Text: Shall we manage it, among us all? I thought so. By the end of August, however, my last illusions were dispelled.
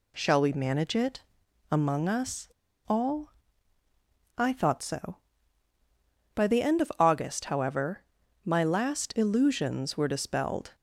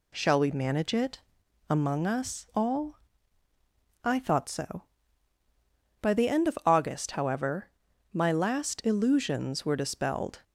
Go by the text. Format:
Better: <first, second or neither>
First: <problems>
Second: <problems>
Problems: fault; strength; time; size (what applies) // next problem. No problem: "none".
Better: second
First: pauses between "us" and "all"; at 2.4 s; 0.40 s long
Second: none